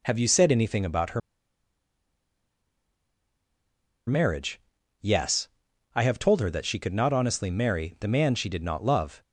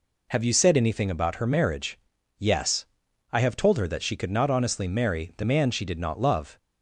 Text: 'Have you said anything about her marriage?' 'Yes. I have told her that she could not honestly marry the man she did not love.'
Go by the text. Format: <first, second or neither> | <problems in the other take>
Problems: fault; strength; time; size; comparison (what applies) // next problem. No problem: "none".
second | pauses between "her" and "marriage"; strong; at 1.2 s; 2.8 s long